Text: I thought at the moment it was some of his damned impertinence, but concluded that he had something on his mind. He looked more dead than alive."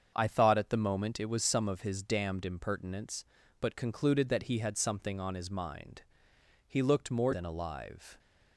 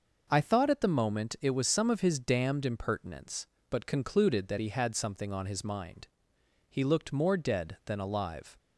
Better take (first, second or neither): second